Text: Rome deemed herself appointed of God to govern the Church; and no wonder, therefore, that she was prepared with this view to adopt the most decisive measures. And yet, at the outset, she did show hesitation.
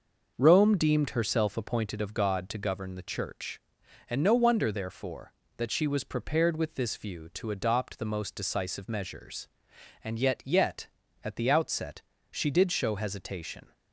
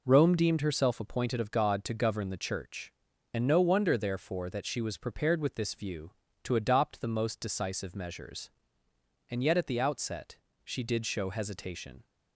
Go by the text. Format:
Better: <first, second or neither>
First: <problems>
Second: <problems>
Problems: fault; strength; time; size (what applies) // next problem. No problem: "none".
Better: second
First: says "yet" twice; at 10.4 s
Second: none